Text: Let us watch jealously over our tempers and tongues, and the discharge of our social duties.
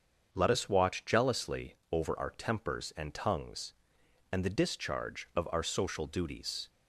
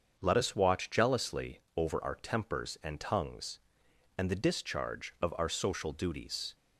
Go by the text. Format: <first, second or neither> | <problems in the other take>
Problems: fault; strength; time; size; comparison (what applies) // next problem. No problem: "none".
neither | starts louder than the rest; the same in both // pauses between "jealously" and "over"; slight; the same in both